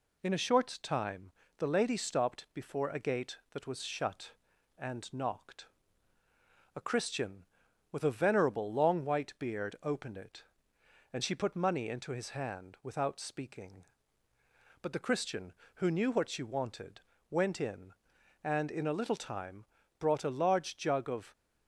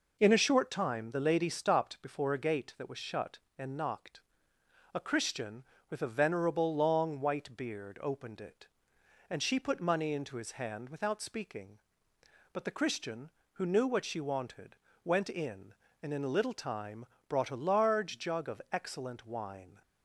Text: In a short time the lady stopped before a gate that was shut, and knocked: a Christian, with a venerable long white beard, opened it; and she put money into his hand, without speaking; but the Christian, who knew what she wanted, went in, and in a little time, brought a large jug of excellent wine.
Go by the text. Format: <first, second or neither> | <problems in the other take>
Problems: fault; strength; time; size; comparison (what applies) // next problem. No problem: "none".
second | pauses between "time" and "the"; slight; at 1.3 s; 0.28 s long // stops before "excellent wine"; at 21.3 s